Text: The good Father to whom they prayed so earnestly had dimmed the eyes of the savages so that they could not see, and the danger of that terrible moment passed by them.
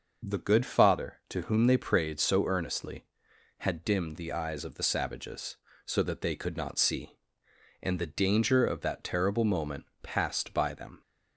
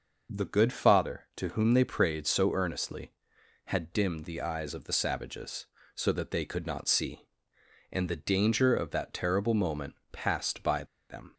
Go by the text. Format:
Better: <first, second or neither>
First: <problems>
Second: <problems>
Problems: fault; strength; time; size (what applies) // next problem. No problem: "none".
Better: first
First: pauses between "moment" and "passed"; slight; at 9.8 s; 0.18 s long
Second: pauses between "moment" and "passed"; slight; at 9.9 s; 0.18 s long // pauses between "by" and "them"; slight; at 10.8 s; 0.25 s long